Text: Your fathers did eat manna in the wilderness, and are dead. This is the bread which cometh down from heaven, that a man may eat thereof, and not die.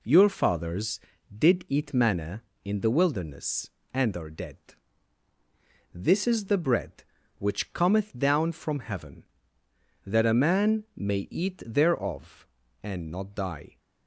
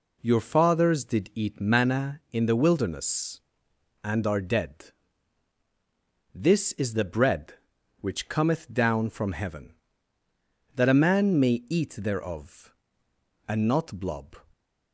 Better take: first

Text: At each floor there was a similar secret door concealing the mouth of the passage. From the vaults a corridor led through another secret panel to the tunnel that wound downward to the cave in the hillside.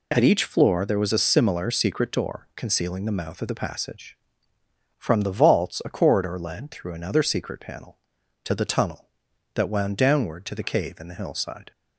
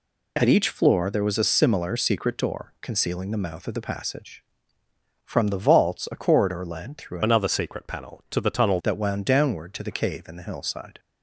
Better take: first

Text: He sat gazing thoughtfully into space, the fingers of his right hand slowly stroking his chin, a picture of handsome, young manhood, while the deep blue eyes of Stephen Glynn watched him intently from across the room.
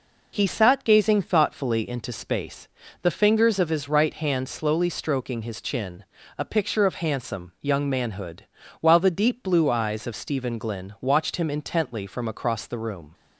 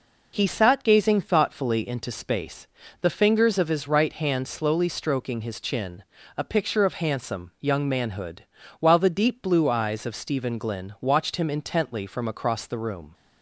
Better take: neither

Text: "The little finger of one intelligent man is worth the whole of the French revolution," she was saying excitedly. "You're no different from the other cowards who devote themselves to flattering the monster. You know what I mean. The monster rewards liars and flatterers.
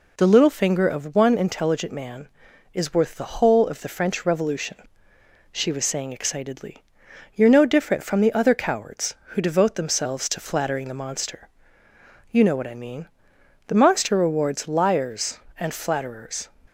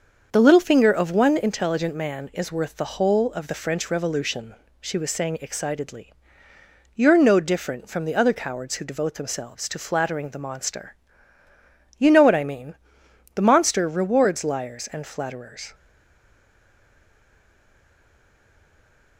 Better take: first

